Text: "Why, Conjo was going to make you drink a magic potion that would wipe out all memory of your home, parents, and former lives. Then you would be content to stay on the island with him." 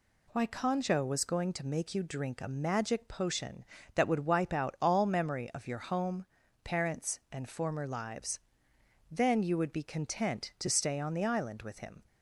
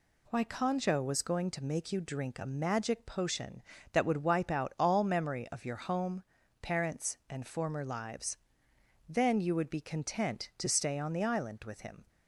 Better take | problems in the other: neither | none

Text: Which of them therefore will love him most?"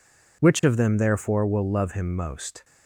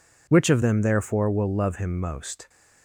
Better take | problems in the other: neither | none

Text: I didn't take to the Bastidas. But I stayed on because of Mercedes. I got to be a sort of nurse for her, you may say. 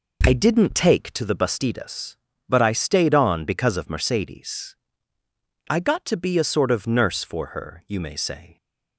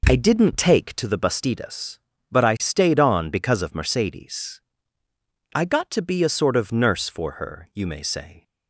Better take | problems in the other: neither | none

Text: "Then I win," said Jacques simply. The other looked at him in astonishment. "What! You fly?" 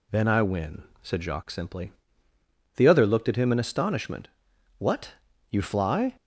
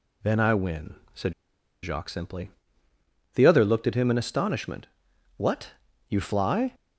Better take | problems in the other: first | pauses between "said" and "Jacques"; noticeable; at 1.3 s; 0.51 s long

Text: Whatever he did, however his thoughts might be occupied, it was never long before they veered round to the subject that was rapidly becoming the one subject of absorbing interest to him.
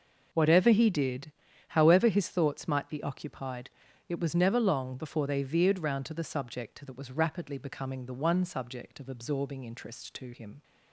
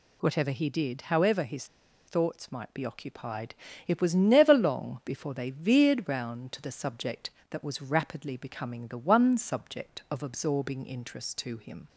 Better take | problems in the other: first | pauses between "his" and "thoughts"; at 1.6 s; 0.42 s long

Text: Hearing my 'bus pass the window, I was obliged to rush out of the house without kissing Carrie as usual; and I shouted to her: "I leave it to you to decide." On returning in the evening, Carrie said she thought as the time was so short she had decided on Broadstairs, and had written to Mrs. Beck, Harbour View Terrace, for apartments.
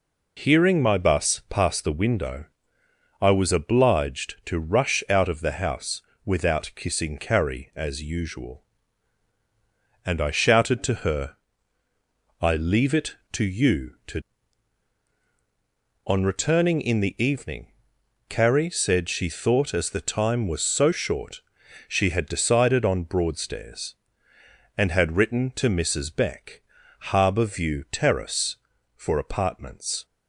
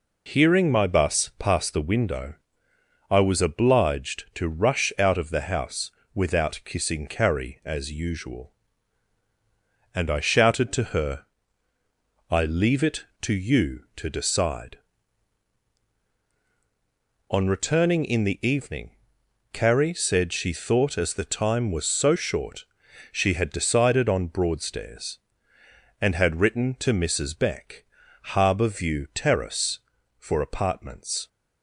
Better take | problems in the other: second | pauses between "house" and "without"; slight; at 5.9 s; 0.26 s long; slight in the second // skips "decide"; at 15.1 s // pauses between "short" and "she"; noticeable; at 21.4 s; 0.48 s long; noticeable in the second

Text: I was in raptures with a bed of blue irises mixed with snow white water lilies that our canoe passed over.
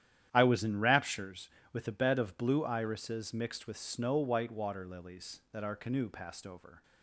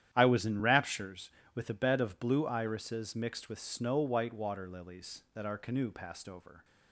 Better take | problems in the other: neither | starts louder than the rest; strong; the same in both

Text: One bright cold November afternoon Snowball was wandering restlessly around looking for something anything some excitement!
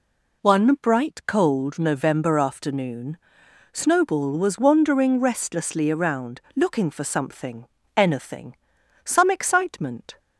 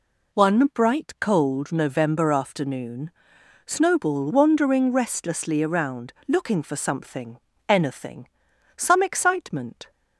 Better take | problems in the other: first | pauses between "afternoon" and "Snowball"; noticeable; at 3.0 s; 0.56 s long; noticeable in the first // skips "was"; at 4.3 s // pauses between "something" and "anything"; slight; at 7.3 s; 0.30 s long; slight in the first // pauses between "anything" and "some"; noticeable; at 8.2 s; 0.48 s long; noticeable in the first

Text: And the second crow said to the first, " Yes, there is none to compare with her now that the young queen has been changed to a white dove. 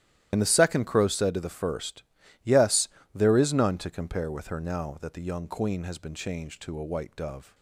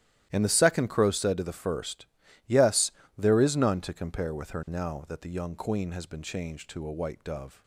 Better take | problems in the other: second | loses the start of "And"; at 0.3 s; 55 ms // starts louder than the rest; strong; until 1.3 s; 12.5 dB; strong in the second

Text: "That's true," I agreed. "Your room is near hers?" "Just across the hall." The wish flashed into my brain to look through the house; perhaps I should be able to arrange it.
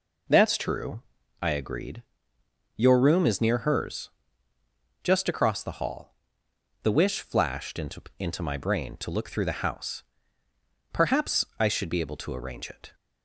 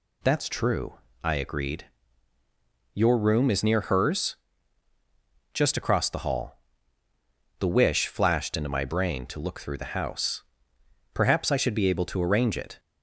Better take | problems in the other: second | says "into" twice; at 8.1 s

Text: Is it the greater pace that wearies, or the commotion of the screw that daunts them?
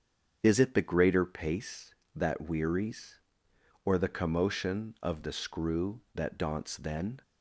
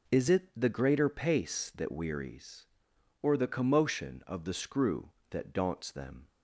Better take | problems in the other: second | starts louder than the rest; strong; until 1.4 s; 7.5 dB // says "then" for "them"; at 6.7 s

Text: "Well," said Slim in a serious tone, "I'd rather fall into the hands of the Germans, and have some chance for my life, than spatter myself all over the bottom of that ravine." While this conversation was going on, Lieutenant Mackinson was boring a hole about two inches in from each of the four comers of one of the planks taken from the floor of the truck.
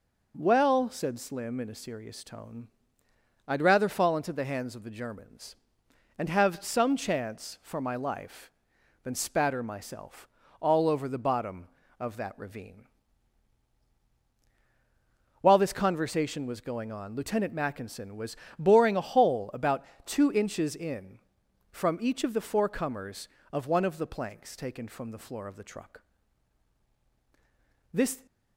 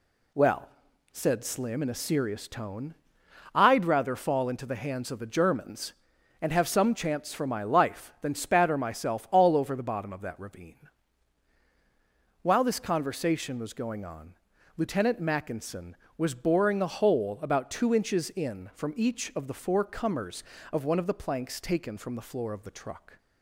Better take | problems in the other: second | pauses between "myself" and "all"; slight; at 10.2 s; 0.32 s long // pauses between "was" and "boring"; slight; at 18.3 s; 0.22 s long // pauses between "about" and "two"; slight; at 19.8 s; 0.20 s long // goes on to say "This"; slight; from 27.9 s on; 0.32 s long

